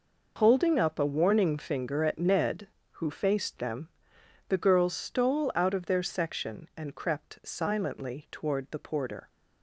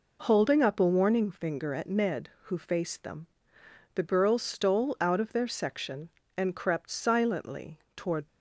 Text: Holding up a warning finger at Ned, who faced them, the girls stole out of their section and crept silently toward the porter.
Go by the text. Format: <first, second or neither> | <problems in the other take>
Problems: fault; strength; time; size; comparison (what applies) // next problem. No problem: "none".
first | pauses between "silently" and "toward"; slight; at 7.7 s; 0.18 s long // stops before "the porter"; at 8.2 s